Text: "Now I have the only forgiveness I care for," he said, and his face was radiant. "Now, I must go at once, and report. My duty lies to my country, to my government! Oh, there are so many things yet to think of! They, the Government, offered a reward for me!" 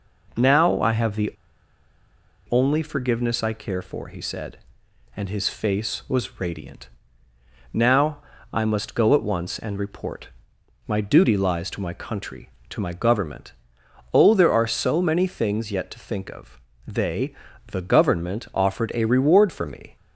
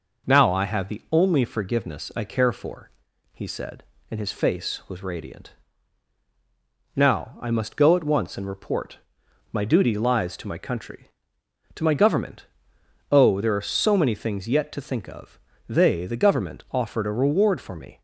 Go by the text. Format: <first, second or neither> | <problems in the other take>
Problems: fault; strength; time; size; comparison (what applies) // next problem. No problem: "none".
second | pauses between "the" and "only"; at 1.3 s; 1.1 s long